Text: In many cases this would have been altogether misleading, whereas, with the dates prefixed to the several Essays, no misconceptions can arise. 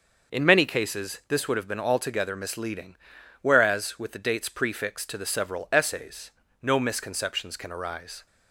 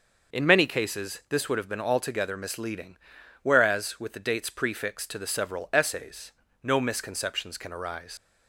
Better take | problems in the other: first | starts louder than the rest; noticeable; until 1.3 s; 6 dB; also in the first // leaves "arise" unfinished; at 8.1 s; 90 ms

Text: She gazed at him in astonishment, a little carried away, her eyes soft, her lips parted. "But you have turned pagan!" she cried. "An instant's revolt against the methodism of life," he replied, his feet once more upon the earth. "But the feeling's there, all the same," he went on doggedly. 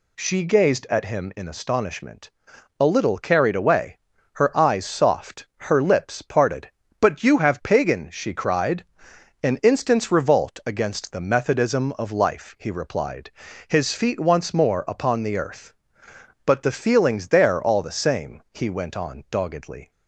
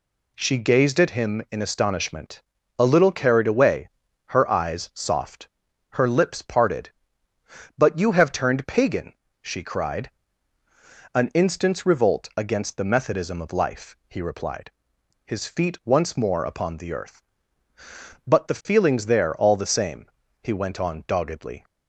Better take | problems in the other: second | skips "turned"; at 7.6 s

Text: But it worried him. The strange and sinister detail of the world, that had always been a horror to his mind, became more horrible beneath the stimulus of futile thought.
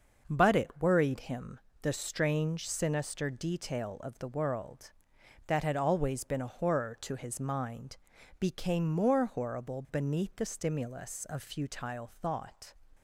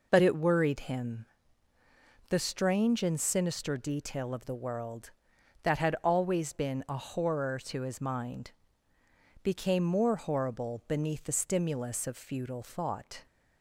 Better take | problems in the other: second | starts louder than the rest; until 1.2 s; 6 dB // skips "and"; at 2.6 s

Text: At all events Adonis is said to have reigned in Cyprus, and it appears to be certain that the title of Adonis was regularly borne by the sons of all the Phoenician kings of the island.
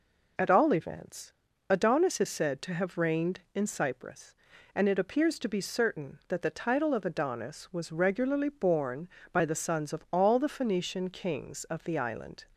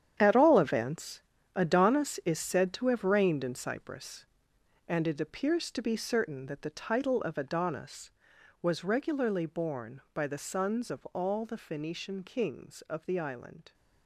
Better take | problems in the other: first | gets quieter; strong; throughout; 12.5 dB // pauses between "events" and "Adonis"; slight; at 1.2 s; 0.34 s long; also in the first

